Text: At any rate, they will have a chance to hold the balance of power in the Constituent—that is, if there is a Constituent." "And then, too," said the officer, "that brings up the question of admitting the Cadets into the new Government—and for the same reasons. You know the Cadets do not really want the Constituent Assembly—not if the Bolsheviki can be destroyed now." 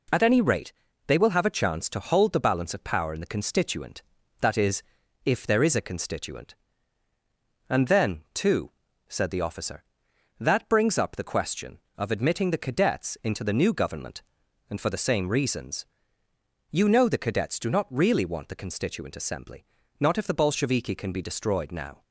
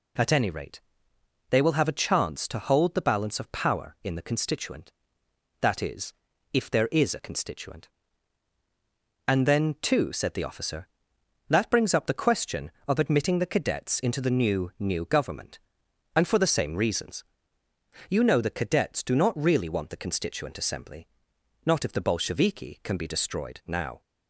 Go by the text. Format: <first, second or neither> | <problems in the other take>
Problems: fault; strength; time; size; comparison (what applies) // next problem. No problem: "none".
first | says "new" twice; at 14.7 s